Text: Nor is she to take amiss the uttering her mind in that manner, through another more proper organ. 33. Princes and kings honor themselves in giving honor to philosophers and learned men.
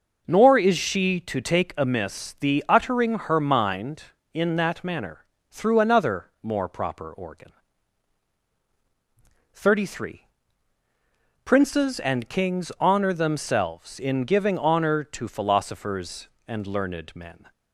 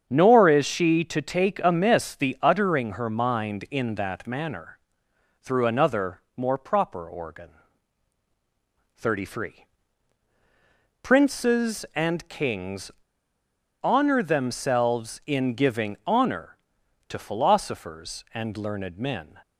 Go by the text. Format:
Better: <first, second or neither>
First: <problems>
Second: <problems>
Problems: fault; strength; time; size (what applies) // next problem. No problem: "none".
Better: first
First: pauses between "another" and "more"; slight; at 6.2 s; 0.16 s long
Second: starts louder than the rest; strong; until 1.1 s; 7.5 dB // pauses between "another" and "more"; slight; at 6.2 s; 0.16 s long // pauses between "kings" and "honor"; noticeable; at 12.9 s; 0.92 s long